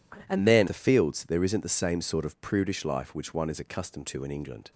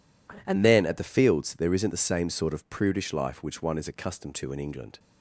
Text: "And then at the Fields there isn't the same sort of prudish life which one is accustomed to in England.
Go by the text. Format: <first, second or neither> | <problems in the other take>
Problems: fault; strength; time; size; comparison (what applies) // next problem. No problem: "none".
second | skips "at"; at 0.6 s